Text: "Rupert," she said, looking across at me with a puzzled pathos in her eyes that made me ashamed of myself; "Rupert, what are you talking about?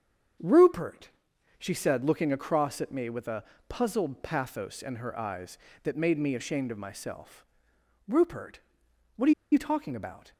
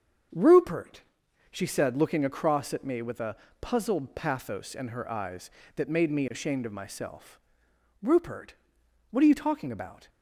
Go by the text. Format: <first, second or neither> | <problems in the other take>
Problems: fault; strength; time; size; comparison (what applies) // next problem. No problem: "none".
second | starts louder than the rest; until 1.9 s; 7 dB; also in the second // pauses between "a" and "puzzled"; slight; at 3.4 s; 0.24 s long; slight in the second // pauses between "are" and "you"; slight; at 9.3 s; 0.20 s long